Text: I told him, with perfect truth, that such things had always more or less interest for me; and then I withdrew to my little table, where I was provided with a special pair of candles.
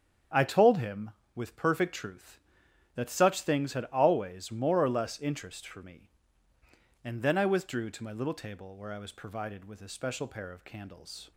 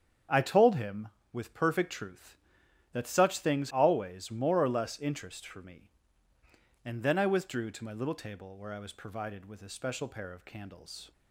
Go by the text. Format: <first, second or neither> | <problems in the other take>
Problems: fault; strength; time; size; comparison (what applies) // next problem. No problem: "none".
first | starts louder than the rest; strong; until 1.5 s; 8 dB; strong in the first // skips "had"; at 3.7 s